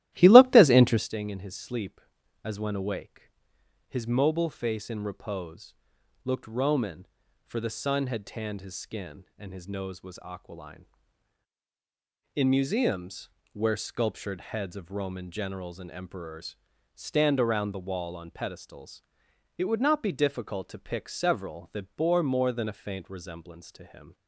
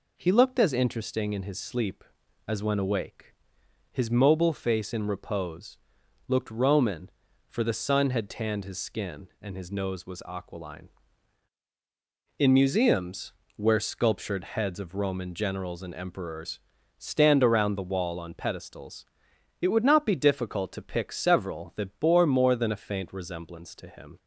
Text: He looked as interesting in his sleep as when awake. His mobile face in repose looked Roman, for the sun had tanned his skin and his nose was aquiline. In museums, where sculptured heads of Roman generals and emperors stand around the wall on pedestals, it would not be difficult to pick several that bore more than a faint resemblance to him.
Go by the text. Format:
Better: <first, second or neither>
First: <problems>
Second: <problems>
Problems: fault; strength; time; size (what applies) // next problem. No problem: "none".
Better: second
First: starts louder than the rest; strong; until 1.1 s; 14.5 dB // pauses between "repose" and "looked"; noticeable; at 5.7 s; 0.50 s long // pauses between "emperors" and "stand"; at 16.5 s; 0.38 s long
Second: pauses between "repose" and "looked"; noticeable; at 5.7 s; 0.50 s long // pauses between "emperors" and "stand"; at 16.5 s; 0.38 s long